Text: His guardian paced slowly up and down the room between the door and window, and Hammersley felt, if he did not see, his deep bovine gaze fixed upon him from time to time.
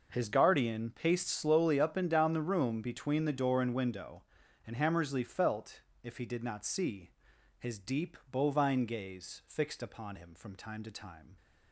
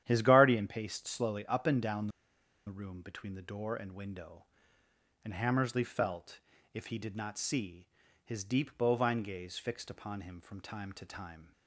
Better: first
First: none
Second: starts louder than the rest; strong; until 1.0 s; 10.5 dB // pauses between "down" and "the"; noticeable; at 2.0 s; 0.58 s long

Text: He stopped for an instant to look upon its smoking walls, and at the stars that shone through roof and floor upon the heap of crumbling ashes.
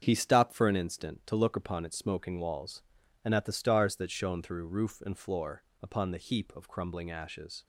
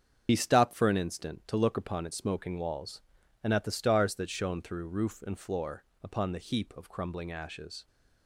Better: first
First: starts louder than the rest; strong; until 1.0 s; 7.5 dB // pauses between "floor" and "upon"; slight; at 5.6 s; 0.18 s long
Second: loses the start of "He"; at 0.2 s; 60 ms // starts louder than the rest; strong; until 1.3 s; 7.5 dB // pauses between "floor" and "upon"; slight; at 5.8 s; 0.18 s long

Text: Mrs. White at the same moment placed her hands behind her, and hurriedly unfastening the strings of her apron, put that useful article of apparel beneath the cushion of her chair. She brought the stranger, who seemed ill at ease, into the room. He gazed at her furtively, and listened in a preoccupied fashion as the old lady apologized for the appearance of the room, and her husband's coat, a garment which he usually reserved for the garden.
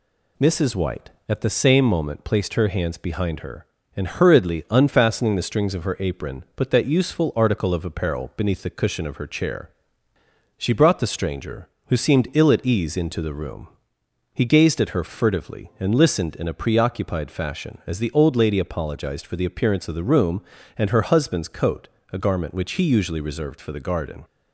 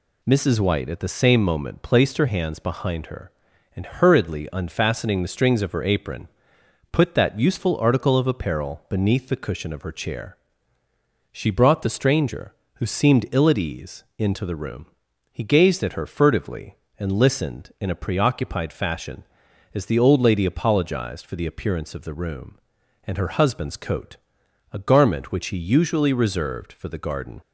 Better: neither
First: none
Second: none

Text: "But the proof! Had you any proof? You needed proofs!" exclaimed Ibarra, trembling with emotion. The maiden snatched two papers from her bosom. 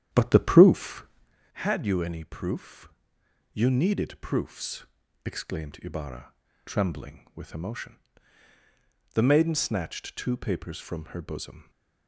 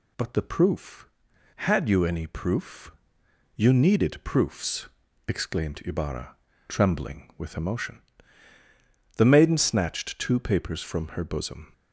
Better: second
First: starts louder than the rest; strong; until 1.3 s; 9.5 dB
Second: none

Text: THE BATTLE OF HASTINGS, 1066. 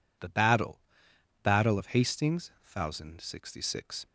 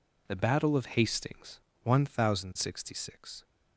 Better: second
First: says "BATTLE" twice; at 1.4 s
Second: none

